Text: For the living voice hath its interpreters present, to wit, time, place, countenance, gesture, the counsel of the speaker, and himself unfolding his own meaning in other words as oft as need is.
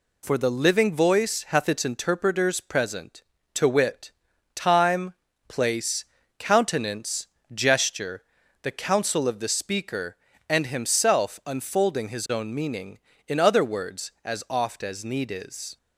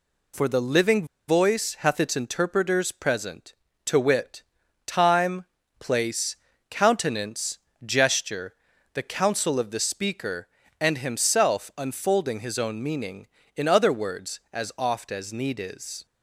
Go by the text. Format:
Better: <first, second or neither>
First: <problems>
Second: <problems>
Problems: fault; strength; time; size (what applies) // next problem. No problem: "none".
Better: first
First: none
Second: pauses between "living" and "voice"; slight; at 1.0 s; 0.21 s long